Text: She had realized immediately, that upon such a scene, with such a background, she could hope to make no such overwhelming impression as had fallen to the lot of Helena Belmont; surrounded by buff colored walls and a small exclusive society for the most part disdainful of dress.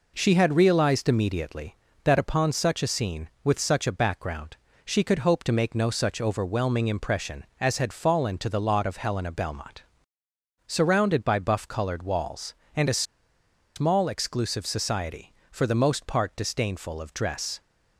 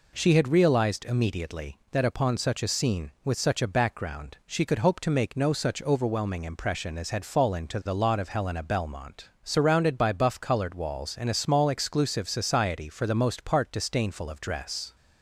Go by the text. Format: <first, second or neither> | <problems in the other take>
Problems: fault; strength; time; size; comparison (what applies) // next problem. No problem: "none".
second | pauses between "a" and "small"; noticeable; at 13.0 s; 0.73 s long